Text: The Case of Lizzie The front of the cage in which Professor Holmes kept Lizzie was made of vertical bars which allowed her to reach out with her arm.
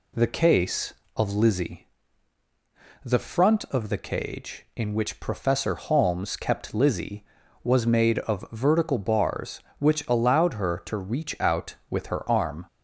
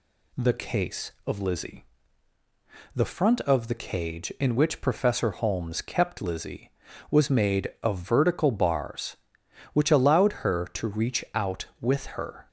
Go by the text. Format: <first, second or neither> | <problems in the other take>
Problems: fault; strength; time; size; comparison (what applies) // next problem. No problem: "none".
first | pauses between "Lizzie" and "The"; at 1.8 s; 1.1 s long; also in the first // stops before "arm"; at 12.4 s